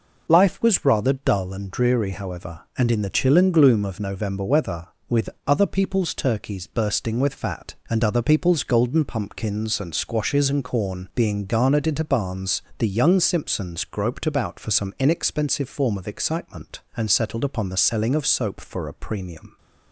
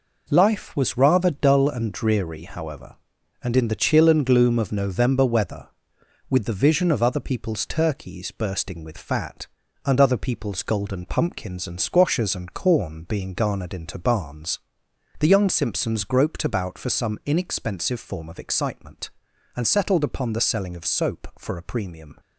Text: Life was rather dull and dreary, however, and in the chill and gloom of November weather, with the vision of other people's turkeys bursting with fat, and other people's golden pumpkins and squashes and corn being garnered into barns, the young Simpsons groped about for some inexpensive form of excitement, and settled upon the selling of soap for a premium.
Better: second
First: skips "the vision of"; at 5.3 s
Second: none

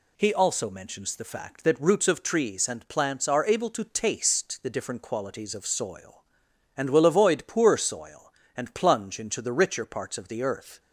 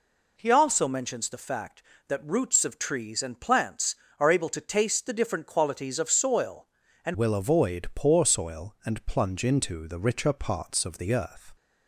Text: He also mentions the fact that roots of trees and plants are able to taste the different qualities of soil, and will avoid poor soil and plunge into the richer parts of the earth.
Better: first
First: none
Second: changes voice at "will"; from 7.1 s on; 4.4 s long

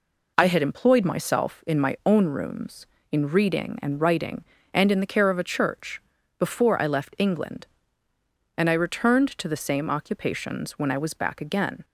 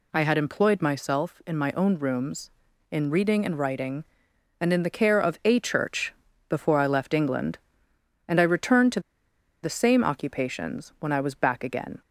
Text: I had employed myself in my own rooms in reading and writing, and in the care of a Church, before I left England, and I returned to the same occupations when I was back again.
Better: first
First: none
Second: pauses between "to" and "the"; noticeable; at 8.9 s; 0.63 s long

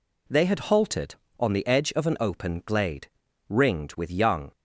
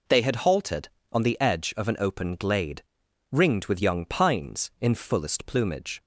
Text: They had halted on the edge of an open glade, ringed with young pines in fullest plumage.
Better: second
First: stops before "pines in fullest plumage"; at 4.5 s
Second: none

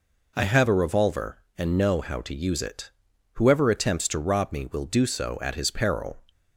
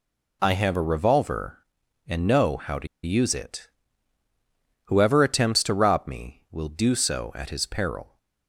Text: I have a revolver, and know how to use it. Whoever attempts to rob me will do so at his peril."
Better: first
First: none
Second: pauses between "to" and "use"; slight; at 2.8 s; 0.18 s long

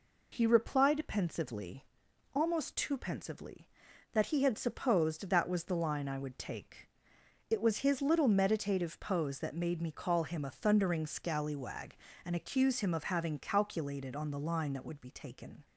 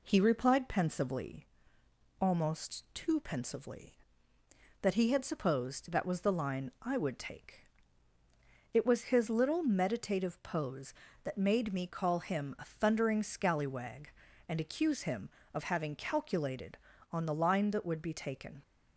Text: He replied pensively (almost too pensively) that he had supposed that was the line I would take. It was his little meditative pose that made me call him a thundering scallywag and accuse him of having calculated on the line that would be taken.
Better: neither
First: none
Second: none

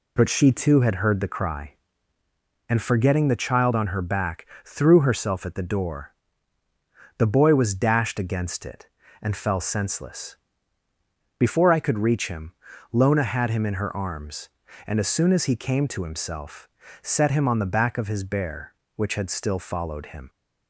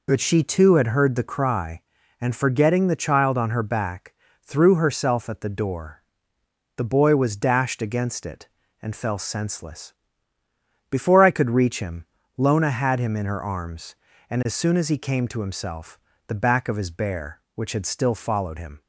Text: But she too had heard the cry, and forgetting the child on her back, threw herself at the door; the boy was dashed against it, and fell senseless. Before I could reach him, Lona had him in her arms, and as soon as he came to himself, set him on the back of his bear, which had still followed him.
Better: first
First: none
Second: skips "set him on"; at 16.1 s

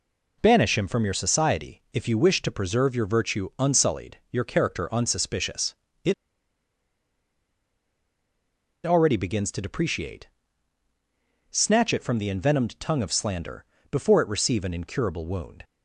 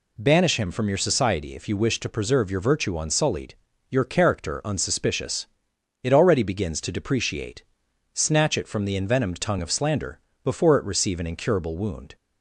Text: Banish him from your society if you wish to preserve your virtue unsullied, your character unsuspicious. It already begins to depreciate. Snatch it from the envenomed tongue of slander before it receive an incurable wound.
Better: second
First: pauses between "It" and "already"; strong; at 6.1 s; 2.7 s long // pauses between "slander" and "before"; slight; at 13.6 s; 0.26 s long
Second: pauses between "slander" and "before"; slight; at 10.1 s; 0.26 s long

